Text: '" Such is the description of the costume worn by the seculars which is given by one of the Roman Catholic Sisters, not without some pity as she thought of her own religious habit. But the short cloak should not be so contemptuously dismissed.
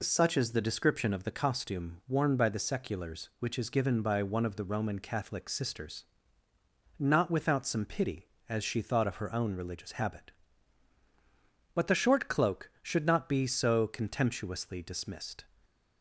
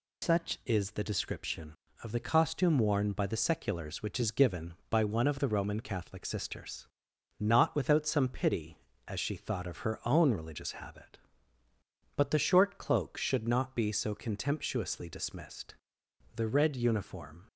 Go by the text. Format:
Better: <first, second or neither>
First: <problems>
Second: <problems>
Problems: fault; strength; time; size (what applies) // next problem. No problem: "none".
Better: first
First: none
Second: goes on to say "The red uniform"; noticeable; from 16.3 s on; 1.1 s long